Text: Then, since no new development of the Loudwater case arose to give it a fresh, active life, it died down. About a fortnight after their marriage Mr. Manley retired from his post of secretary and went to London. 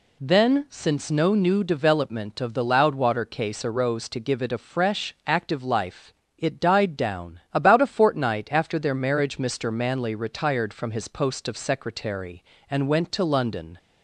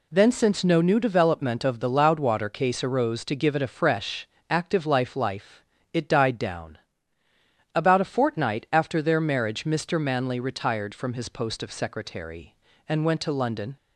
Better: first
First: none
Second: says "life" twice; at 5.1 s

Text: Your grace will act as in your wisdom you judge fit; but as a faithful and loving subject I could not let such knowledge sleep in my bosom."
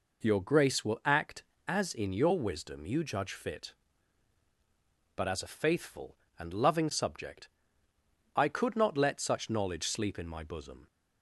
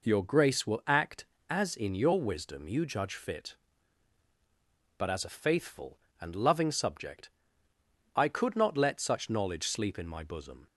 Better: neither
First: pauses between "subject" and "I"; noticeable; at 7.4 s; 0.88 s long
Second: pauses between "subject" and "I"; noticeable; at 7.2 s; 0.86 s long

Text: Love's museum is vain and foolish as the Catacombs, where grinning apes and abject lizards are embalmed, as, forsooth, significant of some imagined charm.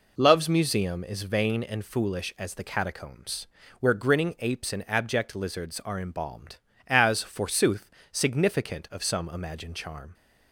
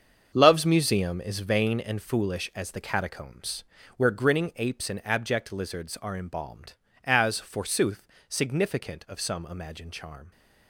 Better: first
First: none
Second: gets quieter; strong; throughout; 10.5 dB

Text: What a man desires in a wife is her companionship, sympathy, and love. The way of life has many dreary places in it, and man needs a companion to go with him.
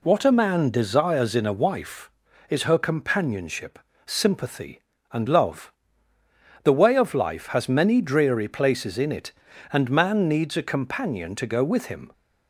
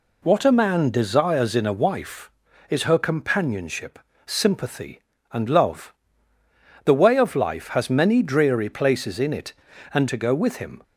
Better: first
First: none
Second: skips "man needs a companion"; at 10.0 s

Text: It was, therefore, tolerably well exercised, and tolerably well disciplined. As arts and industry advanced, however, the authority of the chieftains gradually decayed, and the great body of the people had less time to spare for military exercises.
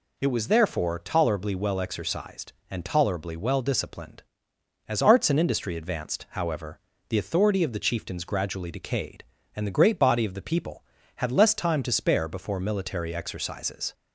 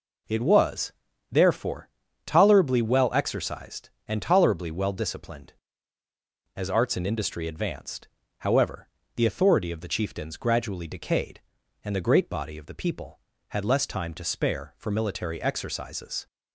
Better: second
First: says "before" for "for"; at 12.2 s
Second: none

